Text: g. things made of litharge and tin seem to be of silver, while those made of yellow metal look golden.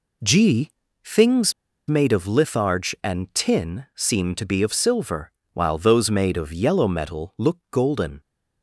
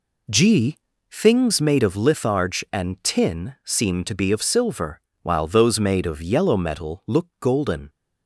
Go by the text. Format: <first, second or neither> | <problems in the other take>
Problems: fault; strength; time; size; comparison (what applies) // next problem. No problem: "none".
second | pauses between "things" and "made"; slight; at 1.5 s; 0.35 s long